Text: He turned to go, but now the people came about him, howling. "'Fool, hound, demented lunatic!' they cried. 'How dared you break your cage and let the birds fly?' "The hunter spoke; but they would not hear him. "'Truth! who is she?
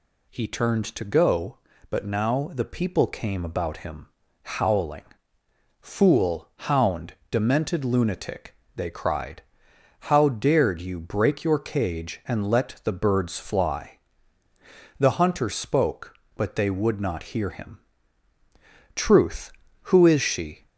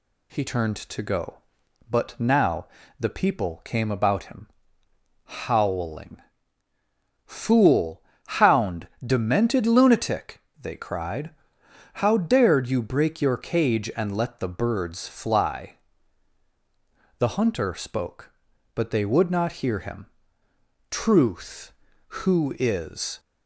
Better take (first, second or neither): first